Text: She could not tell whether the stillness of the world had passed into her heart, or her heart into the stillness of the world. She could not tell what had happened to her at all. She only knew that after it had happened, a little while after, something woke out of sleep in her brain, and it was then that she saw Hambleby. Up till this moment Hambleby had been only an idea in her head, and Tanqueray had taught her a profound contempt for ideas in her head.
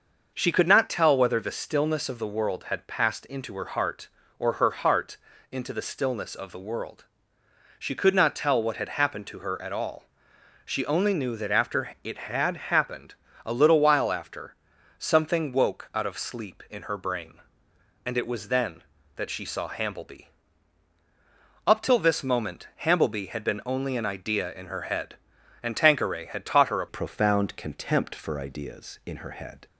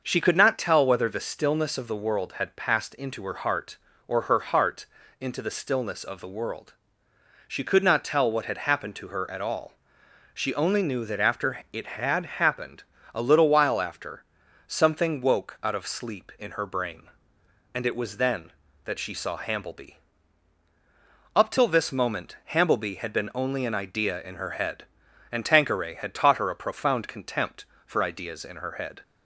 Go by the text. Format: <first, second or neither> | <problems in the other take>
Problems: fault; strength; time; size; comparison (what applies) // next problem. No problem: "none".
second | starts louder than the rest; until 1.3 s; 6 dB; also in the second // pauses between "heart" and "into"; slight; at 5.1 s; 0.36 s long; slight in the second // pauses between "moment" and "Hambleby"; slight; at 22.6 s; 0.16 s long; slight in the second // changes voice at "profound"; from 26.8 s on; 2.8 s long